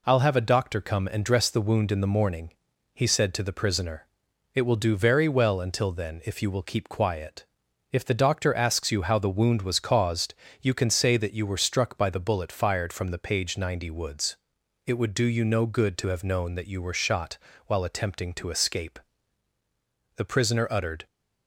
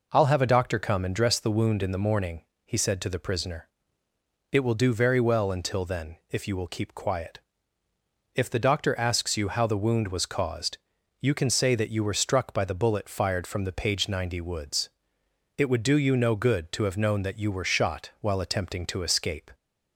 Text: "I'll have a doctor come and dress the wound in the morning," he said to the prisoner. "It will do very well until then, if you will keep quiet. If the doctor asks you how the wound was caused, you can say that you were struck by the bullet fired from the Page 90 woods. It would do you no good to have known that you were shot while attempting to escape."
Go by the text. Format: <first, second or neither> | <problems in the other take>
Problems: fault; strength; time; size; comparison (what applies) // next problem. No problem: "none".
second | pauses between "shot" and "while"; slight; at 17.3 s; 0.30 s long // goes on to say "The prisoner uttered"; noticeable; from 20.1 s on; 0.90 s long